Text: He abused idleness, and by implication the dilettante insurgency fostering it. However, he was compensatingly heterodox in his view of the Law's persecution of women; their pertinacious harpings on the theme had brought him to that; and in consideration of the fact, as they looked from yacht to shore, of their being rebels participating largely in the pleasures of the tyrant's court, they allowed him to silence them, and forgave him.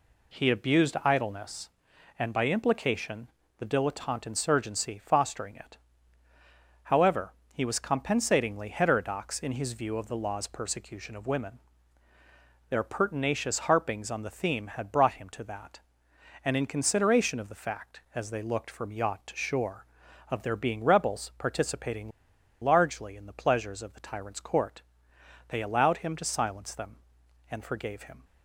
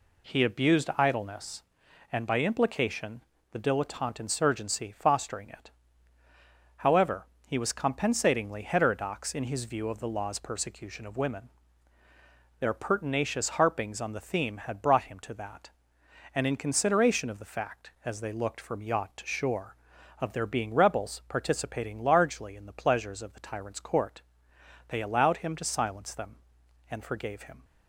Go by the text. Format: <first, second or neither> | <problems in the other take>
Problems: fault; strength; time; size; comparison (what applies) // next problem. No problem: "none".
second | pauses between "implication" and "the"; slight; at 3.2 s; 0.30 s long; slight in the second // pauses between "participating" and "largely"; noticeable; at 22.1 s; 0.53 s long